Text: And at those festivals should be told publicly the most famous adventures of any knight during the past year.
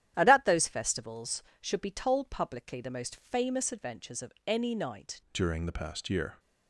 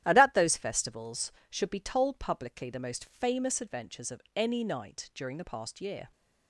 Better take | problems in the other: second | starts louder than the rest; strong; until 1.1 s; 11 dB; strong in the second // changes voice at "during"; from 5.3 s on; 1.0 s long

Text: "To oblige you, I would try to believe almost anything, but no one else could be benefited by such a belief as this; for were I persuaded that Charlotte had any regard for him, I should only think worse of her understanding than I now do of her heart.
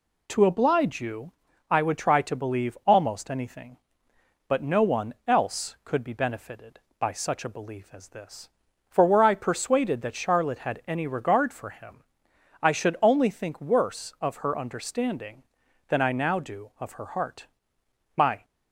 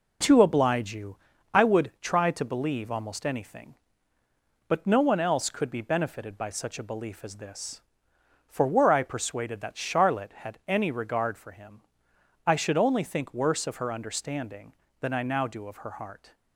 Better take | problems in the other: second | goes on to say "My"; slight; from 18.1 s on; 0.28 s long

